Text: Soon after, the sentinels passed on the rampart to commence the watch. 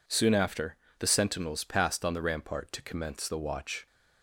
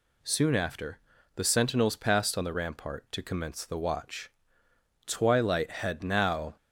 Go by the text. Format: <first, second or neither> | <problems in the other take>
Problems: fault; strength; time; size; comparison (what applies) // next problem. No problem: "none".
first | goes on to say "Twilight had now"; from 5.0 s on; 1.5 s long